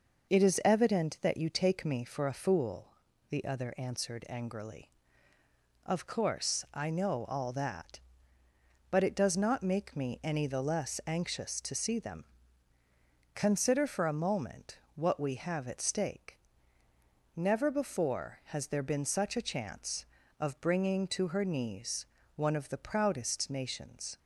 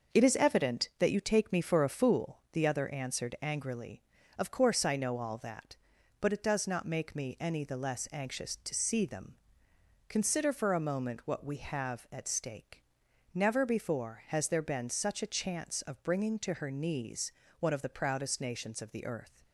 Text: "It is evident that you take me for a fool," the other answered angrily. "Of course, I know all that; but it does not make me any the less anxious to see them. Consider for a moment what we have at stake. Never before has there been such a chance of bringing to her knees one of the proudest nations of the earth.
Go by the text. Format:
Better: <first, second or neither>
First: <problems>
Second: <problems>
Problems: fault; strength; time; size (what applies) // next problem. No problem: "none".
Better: second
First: pauses between "moment" and "what"; slight; at 14.7 s; 0.18 s long // pauses between "knees" and "one"; slight; at 22.0 s; 0.32 s long // stops before "of the earth"; at 24.1 s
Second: pauses between "knees" and "one"; slight; at 17.3 s; 0.30 s long